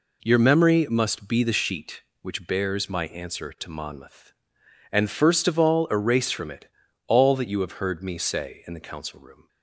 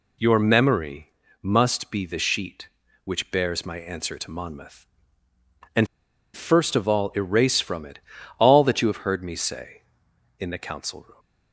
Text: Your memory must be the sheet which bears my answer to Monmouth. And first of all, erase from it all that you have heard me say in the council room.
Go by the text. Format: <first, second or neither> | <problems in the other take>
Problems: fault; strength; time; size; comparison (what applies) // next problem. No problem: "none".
first | pauses between "memory" and "must"; slight; at 1.1 s; 0.30 s long // pauses between "And" and "first"; noticeable; at 5.8 s; 0.48 s long // pauses between "it" and "all"; at 7.9 s; 0.40 s long; also in the first